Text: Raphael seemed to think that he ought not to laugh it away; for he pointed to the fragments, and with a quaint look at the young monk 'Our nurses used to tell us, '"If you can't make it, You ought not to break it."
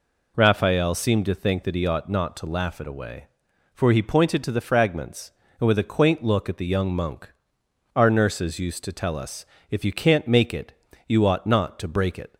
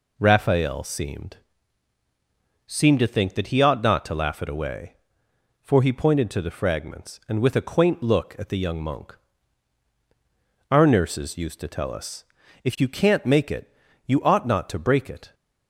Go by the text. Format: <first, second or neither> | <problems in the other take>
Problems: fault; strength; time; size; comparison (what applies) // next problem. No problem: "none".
first | says "seemed" twice; at 2.6 s // pauses between "monk" and "Our"; strong; at 9.1 s; 1.5 s long; noticeable in the first